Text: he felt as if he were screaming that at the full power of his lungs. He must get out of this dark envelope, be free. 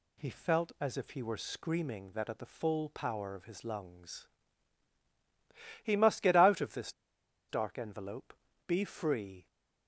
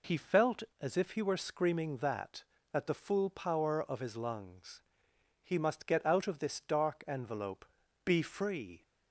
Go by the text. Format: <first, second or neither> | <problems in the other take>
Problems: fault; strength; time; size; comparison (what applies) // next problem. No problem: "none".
second | pauses between "this" and "dark"; noticeable; at 6.9 s; 0.58 s long